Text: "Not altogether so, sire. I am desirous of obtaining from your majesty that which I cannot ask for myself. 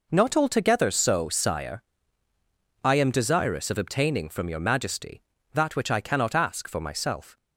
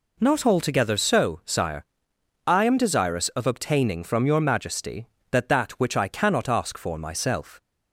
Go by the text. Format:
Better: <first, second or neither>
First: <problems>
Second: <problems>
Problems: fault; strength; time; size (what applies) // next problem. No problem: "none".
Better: first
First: none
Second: says "that" twice; at 5.4 s